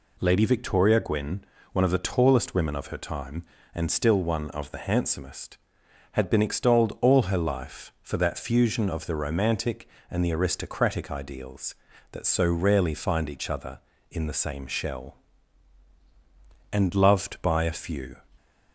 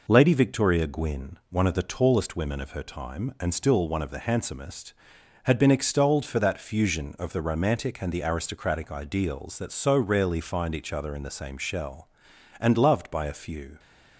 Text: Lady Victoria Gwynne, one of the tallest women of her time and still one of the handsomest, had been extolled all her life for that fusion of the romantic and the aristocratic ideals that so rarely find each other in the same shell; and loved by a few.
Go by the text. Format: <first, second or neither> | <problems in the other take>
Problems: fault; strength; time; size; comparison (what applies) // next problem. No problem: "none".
first | skips "all her life"; at 6.2 s